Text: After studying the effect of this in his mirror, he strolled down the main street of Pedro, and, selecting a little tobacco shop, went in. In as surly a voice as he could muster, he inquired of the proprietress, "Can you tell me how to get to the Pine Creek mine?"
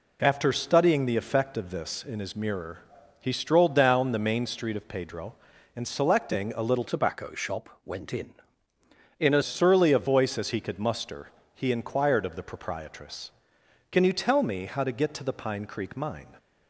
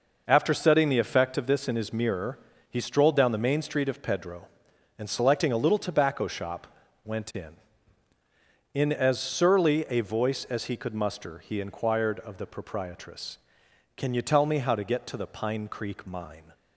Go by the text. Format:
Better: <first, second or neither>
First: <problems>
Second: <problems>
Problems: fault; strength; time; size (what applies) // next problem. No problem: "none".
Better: second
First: changes voice from "tobacco" to "as"; from 6.8 to 9.4 s; 2.6 s long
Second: none